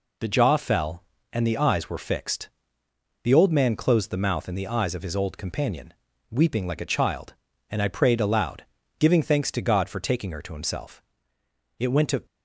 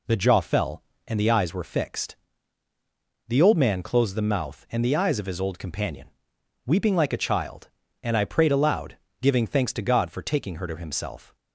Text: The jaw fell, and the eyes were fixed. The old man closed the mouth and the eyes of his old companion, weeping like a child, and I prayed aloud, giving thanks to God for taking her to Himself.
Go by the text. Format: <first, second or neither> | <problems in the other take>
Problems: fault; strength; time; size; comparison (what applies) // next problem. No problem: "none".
second | goes on to say "It went to"; slight; from 11.7 s on; 0.46 s long